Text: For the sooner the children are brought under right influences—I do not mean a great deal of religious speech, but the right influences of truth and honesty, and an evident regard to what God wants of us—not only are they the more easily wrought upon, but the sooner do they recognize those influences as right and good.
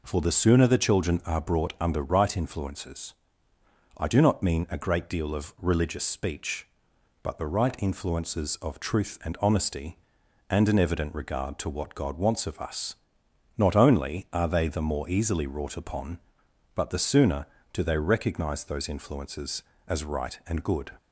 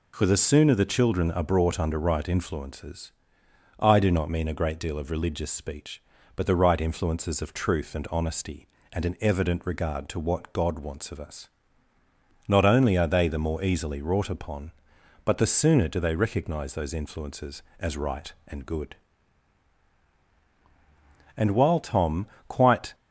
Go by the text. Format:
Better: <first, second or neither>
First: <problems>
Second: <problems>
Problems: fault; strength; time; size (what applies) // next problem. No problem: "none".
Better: first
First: none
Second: goes on to say "And while Tom quite"; from 21.3 s on; 1.6 s long